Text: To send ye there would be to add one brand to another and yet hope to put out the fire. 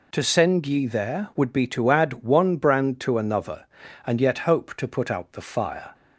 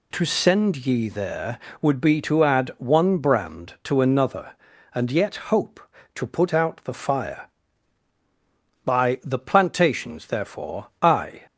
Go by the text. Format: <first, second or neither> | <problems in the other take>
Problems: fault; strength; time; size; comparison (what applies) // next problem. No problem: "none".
first | goes on to say "By the Plantations therefore I"; strong; from 8.8 s on; 2.6 s long